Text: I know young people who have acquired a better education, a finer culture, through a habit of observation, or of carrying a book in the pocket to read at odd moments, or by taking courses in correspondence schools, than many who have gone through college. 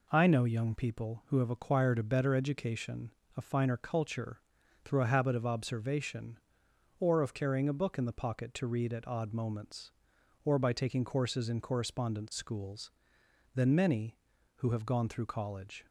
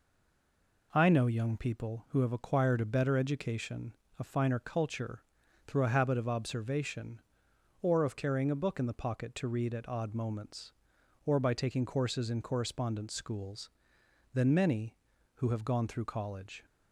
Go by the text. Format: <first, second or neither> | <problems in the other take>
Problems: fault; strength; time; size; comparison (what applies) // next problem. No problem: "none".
first | stays silent before the first word; slight; until 0.9 s; 0.9 s long